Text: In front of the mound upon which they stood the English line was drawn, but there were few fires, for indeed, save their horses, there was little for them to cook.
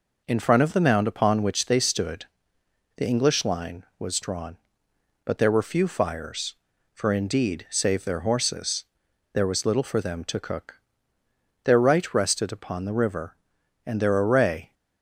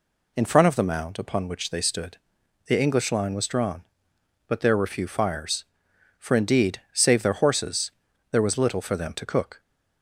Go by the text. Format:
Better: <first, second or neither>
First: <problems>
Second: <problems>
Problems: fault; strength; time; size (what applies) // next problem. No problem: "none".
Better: second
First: pauses between "stood" and "the"; noticeable; at 2.2 s; 0.70 s long // goes on to say "Their right rested upon the river and their array"; strong; from 11.6 s on; 3.1 s long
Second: pauses between "stood" and "the"; noticeable; at 2.1 s; 0.50 s long